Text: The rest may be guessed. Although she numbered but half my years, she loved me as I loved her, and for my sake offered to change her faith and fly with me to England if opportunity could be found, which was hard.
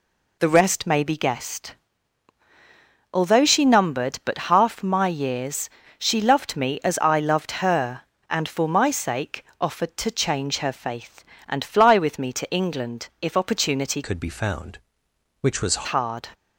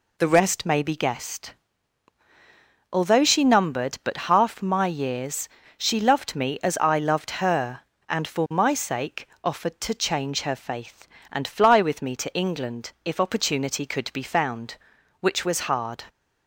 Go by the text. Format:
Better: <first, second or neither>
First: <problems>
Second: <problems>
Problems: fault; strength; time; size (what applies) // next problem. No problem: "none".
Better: second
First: pauses between "sake" and "offered"; slight; at 9.4 s; 0.16 s long // changes voice from "could" to "was"; from 14.0 to 15.8 s; 1.8 s long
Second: pauses between "sake" and "offered"; slight; at 9.2 s; 0.16 s long